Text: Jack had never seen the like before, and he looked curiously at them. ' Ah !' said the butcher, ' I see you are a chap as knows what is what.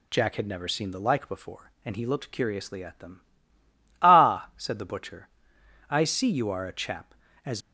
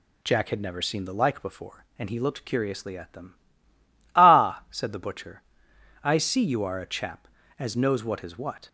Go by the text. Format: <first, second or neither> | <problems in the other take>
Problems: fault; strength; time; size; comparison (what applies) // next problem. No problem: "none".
second | stops before "knows what is what"; at 7.6 s